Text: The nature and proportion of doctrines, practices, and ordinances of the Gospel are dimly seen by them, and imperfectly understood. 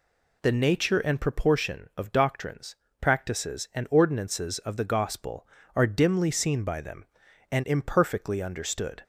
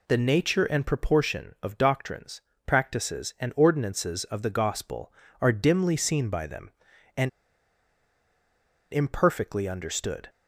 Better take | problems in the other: first | pauses between "and" and "imperfectly"; strong; at 7.2 s; 1.6 s long

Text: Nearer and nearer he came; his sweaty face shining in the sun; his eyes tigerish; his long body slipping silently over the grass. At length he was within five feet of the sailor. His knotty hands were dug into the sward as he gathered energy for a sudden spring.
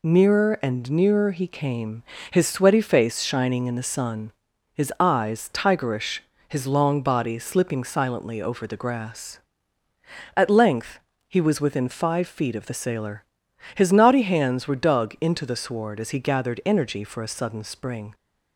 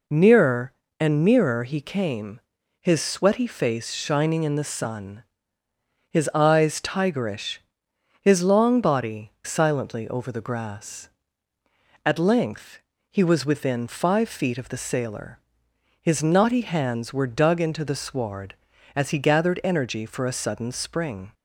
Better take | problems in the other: first | skips "slipping"; at 9.3 s // pauses between "length" and "he"; slight; at 12.7 s; 0.32 s long; slight in the first

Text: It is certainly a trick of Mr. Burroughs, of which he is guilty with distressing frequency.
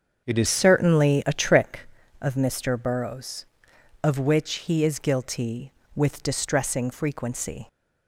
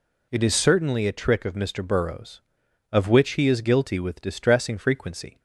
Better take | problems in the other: second | starts louder than the rest; until 1.3 s; 7 dB // changes voice at "certainly"; from 0.4 s on; 7.2 s long

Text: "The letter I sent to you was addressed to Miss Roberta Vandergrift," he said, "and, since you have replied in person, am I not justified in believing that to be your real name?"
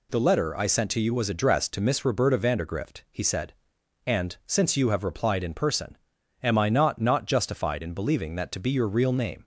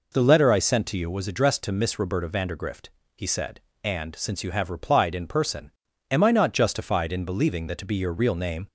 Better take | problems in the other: second | says "not" twice; at 7.0 s

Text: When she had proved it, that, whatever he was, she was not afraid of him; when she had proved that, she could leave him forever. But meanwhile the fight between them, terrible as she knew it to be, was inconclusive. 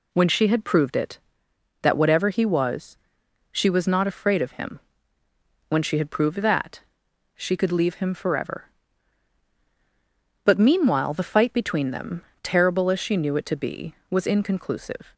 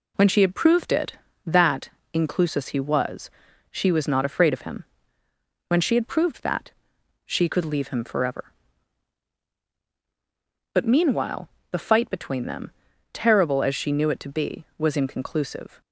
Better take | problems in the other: first | says "inclusus" for "whatever"; at 2.1 s // pauses between "meanwhile" and "the"; slight; at 11.4 s; 0.22 s long

